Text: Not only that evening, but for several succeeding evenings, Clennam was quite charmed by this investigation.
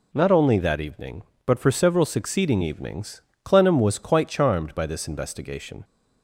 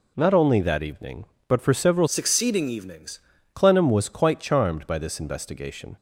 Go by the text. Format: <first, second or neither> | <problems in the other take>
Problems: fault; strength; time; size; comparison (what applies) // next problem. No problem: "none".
first | changes voice from "succeeding" to "evenings"; from 2.0 to 3.2 s; 1.2 s long